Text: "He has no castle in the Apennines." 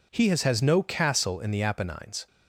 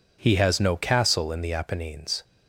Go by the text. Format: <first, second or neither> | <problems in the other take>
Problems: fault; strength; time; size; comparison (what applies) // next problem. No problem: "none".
second | says "has" twice; at 0.4 s